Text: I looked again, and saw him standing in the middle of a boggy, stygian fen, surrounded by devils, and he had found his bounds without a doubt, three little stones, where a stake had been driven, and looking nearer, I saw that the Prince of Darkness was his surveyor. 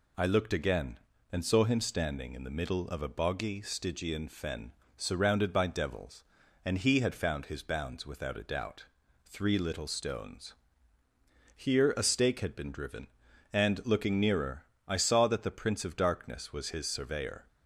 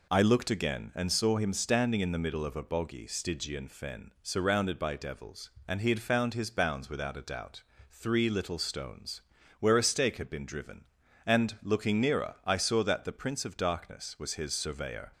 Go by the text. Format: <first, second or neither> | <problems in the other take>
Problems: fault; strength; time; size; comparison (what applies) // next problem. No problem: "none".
second | says "here" for "where"; at 11.5 s